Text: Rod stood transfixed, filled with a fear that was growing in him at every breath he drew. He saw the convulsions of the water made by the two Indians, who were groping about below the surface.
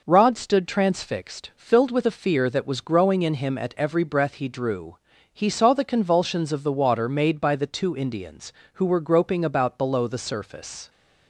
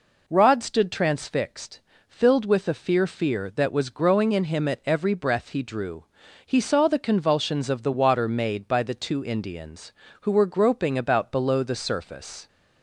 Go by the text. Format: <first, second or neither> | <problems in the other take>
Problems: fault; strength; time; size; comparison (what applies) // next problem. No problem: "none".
first | says "fear" twice; at 3.0 s